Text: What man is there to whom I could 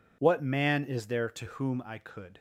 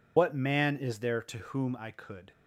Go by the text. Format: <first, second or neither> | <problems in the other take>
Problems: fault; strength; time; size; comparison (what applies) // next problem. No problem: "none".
first | loses the start of "What"; at 0.1 s; 55 ms